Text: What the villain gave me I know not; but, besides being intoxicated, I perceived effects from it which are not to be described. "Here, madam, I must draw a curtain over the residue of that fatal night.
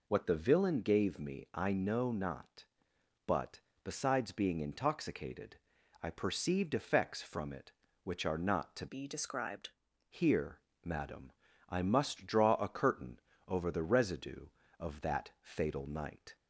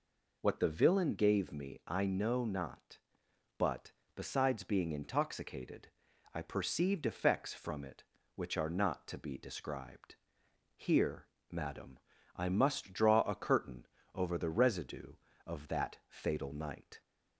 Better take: second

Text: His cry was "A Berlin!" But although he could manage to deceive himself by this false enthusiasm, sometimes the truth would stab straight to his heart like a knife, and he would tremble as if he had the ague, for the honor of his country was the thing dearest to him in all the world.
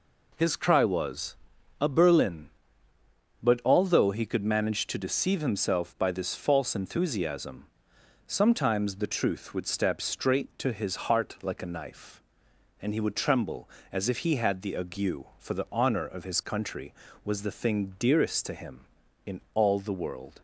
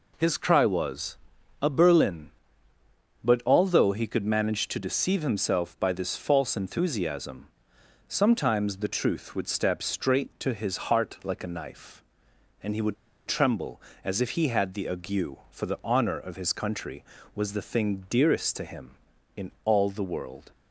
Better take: first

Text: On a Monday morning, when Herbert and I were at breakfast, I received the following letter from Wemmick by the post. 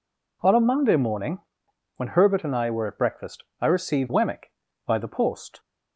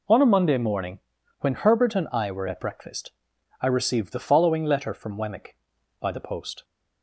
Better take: second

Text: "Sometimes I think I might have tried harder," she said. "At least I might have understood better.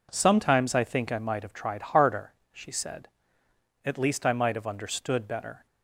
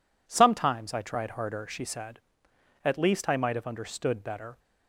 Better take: first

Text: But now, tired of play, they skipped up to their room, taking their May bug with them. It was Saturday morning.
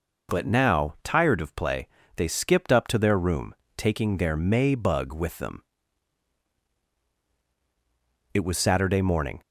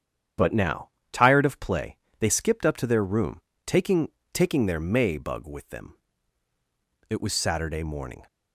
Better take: first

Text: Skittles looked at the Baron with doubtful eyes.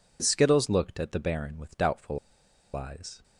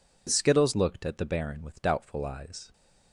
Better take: second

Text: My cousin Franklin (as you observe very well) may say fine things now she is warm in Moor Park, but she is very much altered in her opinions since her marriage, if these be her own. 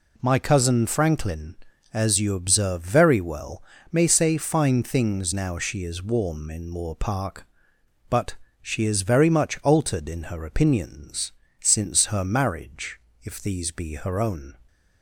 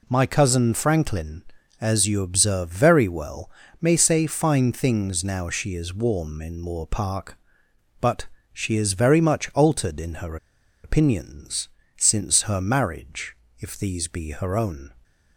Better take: first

